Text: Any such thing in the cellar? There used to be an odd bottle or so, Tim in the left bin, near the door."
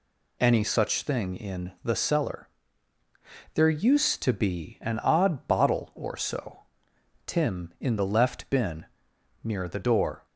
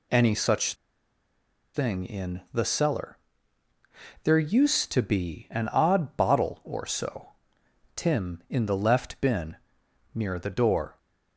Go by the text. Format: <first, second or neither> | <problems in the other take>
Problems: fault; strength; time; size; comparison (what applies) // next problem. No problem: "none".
first | pauses between "such" and "thing"; at 0.7 s; 1.0 s long